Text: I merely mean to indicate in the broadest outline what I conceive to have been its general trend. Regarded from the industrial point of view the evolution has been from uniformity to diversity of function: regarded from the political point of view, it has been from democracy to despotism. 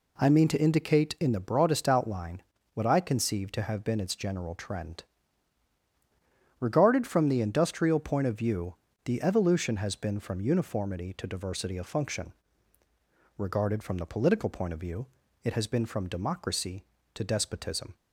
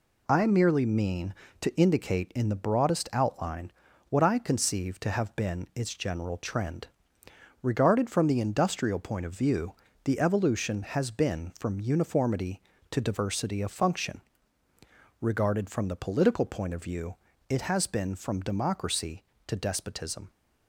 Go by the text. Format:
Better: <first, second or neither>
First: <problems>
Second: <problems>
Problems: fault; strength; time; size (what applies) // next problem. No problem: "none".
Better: second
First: skips "merely"; at 0.3 s // pauses between "outline" and "what"; slight; at 2.4 s; 0.32 s long // pauses between "view" and "the"; slight; at 8.7 s; 0.30 s long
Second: pauses between "outline" and "what"; at 3.6 s; 0.40 s long // pauses between "view" and "the"; slight; at 9.7 s; 0.28 s long